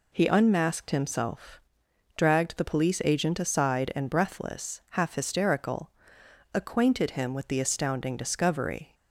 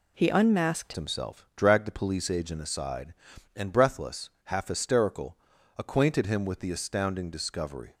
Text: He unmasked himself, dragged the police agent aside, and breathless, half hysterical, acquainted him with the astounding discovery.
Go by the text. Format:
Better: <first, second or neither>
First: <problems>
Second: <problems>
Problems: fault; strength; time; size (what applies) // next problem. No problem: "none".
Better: first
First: none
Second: changes voice at "himself"; from 0.9 s on; 7.0 s long